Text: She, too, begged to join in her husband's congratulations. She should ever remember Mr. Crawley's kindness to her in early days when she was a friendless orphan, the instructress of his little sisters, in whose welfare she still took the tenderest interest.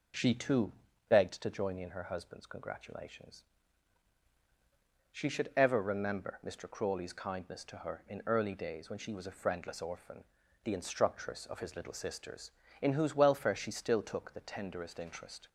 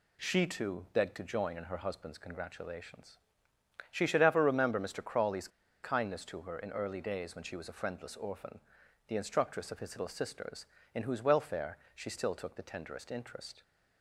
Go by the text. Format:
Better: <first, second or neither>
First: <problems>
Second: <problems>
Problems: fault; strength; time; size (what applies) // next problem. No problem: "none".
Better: first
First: none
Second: pauses between "Crawley's" and "kindness"; slight; at 5.4 s; 0.35 s long // pauses between "welfare" and "she"; slight; at 11.7 s; 0.16 s long